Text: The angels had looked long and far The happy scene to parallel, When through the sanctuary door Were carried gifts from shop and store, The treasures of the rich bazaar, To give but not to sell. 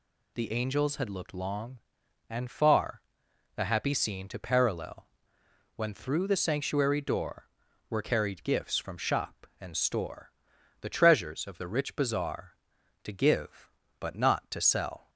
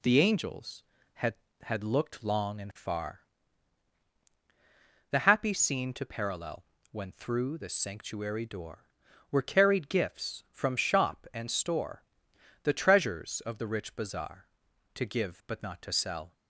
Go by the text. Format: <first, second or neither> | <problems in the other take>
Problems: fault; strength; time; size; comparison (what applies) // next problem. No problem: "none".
first | says "had" twice; at 1.6 s // pauses between "far" and "The"; strong; at 3.2 s; 1.8 s long; noticeable in the first